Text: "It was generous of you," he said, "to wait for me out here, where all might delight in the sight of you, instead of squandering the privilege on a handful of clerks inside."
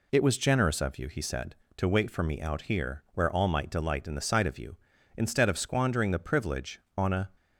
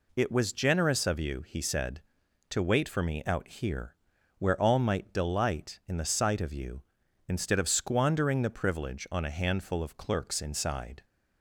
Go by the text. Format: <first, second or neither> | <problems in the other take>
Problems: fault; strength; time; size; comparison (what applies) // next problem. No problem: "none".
second | stops before "handful of clerks inside"; at 7.3 s